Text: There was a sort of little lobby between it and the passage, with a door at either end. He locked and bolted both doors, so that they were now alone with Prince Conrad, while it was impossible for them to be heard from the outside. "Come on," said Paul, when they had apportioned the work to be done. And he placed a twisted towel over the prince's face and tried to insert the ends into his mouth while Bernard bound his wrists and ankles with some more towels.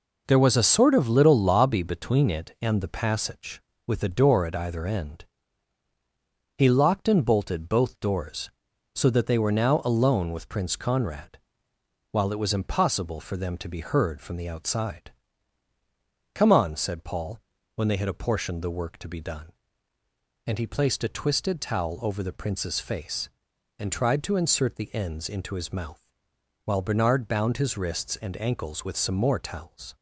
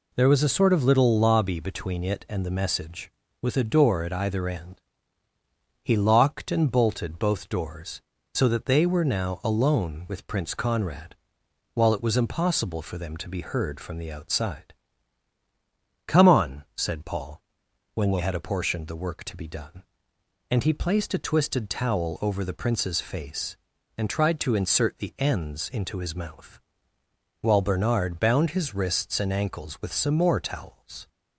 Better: first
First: pauses between "mouth" and "while"; noticeable; at 26.0 s; 0.64 s long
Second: says "message" for "passage"; at 2.4 s // pauses between "mouth" and "while"; noticeable; at 26.5 s; 0.82 s long

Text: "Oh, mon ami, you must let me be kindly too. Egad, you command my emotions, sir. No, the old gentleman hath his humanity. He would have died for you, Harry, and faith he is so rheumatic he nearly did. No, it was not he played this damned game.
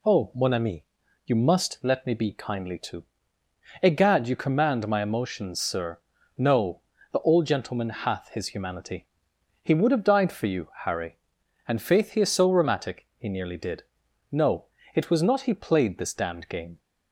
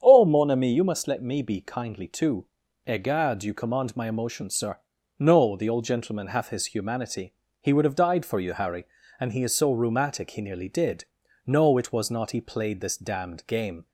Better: first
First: none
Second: starts louder than the rest; strong; until 1.0 s; 8.5 dB // skips "faith"; at 9.3 s

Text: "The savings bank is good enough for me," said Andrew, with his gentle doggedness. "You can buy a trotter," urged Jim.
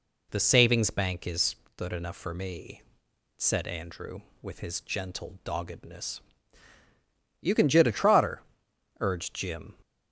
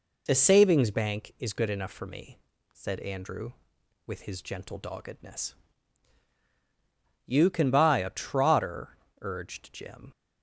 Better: second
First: pauses between "is" and "good"; slight; at 1.5 s; 0.20 s long // says "jit" for "buy"; at 7.6 s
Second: none

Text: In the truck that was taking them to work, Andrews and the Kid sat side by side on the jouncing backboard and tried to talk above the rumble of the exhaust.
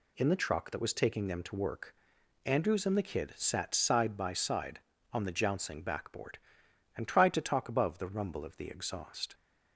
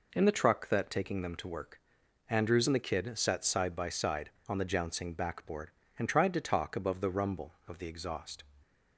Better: first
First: none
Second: skips "was"; at 0.8 s

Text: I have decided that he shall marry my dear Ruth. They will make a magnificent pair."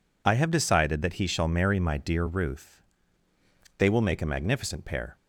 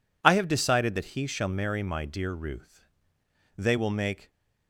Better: first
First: none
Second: stops before "a magnificent pair"; at 4.2 s

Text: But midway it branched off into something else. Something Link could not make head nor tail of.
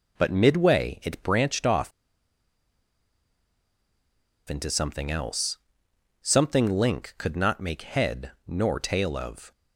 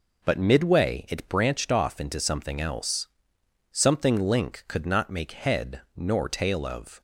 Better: second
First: pauses between "off" and "into"; strong; at 1.9 s; 2.5 s long // pauses between "head" and "nor"; slight; at 8.3 s; 0.16 s long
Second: pauses between "head" and "nor"; slight; at 5.8 s; 0.15 s long

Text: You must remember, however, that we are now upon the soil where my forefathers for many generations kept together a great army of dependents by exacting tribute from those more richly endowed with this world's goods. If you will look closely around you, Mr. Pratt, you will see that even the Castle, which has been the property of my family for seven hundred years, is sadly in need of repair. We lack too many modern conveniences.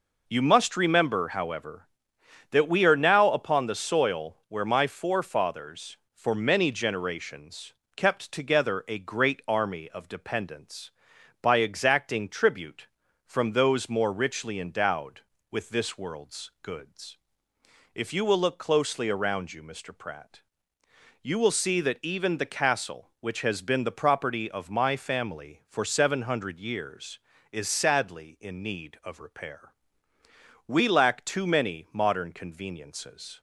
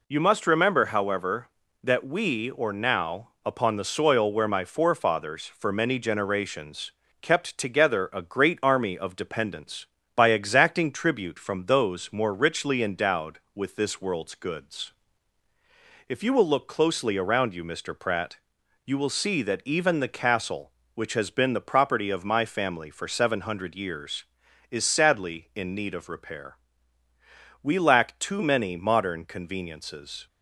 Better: first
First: pauses between "generations" and "kept"; slight; at 7.7 s; 0.22 s long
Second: says "or" for "are"; at 2.5 s // pauses between "generations" and "kept"; slight; at 6.9 s; 0.28 s long

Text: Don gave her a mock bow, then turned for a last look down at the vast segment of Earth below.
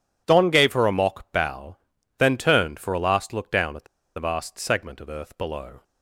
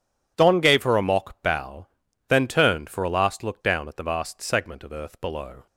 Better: second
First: pauses between "the" and "vast"; slight; at 3.8 s; 0.32 s long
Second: none

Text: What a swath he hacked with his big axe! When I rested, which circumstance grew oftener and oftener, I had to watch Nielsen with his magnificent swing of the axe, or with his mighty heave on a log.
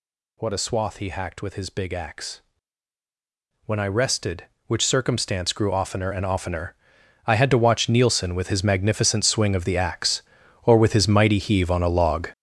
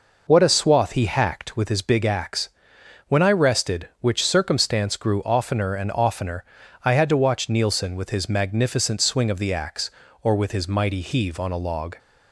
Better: second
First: gets louder; strong; throughout; 10.5 dB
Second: none

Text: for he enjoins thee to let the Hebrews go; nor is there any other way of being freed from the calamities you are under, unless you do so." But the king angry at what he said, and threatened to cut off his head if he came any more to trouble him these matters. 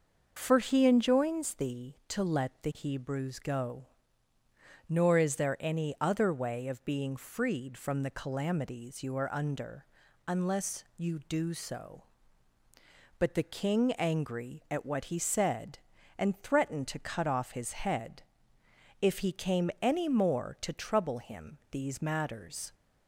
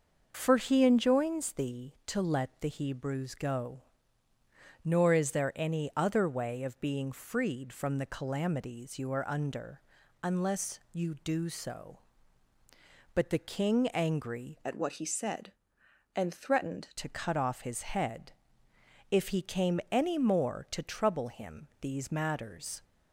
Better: first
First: starts louder than the rest; noticeable; until 1.3 s; 6 dB // pauses between "head" and "if"; noticeable; at 18.2 s; 0.80 s long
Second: starts louder than the rest; noticeable; until 1.3 s; 6 dB // changes voice from "at" to "threatened"; from 14.6 to 16.9 s; 2.3 s long // pauses between "head" and "if"; noticeable; at 18.3 s; 0.80 s long

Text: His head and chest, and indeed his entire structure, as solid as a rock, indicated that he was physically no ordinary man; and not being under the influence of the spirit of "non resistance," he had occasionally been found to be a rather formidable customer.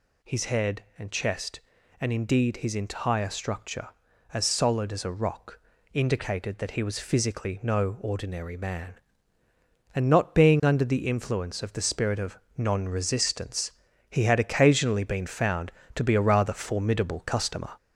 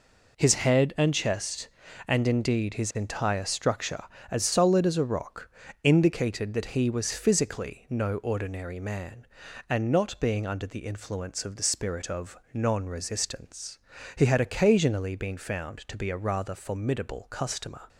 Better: second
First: gets louder; throughout; 4 dB // pauses between "of" and "non"; slight; at 12.3 s; 0.18 s long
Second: pauses between "of" and "non"; slight; at 12.3 s; 0.18 s long

